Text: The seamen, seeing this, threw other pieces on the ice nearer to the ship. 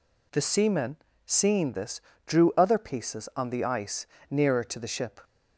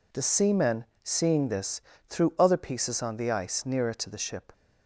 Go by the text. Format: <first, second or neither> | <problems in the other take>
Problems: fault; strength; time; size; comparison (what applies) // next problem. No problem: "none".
second | says "drew" for "threw"; at 2.2 s // pauses between "ice" and "nearer"; slight; at 4.0 s; 0.24 s long